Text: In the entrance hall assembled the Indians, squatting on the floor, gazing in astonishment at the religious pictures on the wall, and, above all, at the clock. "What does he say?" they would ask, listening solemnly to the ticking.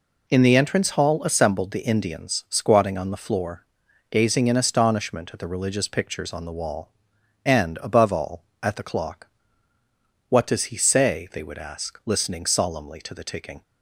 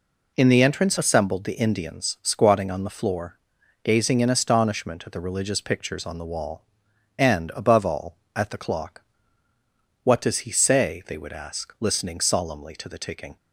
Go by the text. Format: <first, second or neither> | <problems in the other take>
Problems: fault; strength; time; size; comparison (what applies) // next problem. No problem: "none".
first | skips "hall"; at 0.9 s